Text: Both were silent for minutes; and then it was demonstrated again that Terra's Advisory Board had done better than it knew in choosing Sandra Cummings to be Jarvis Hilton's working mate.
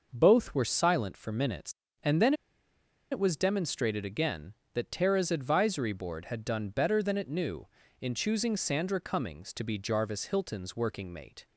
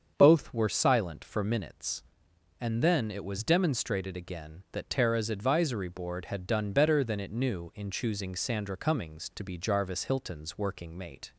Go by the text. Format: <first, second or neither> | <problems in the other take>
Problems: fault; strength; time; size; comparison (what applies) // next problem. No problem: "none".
second | starts louder than the rest; noticeable; until 1.1 s; 6 dB; strong in the second // pauses between "then" and "it"; noticeable; at 2.3 s; 0.78 s long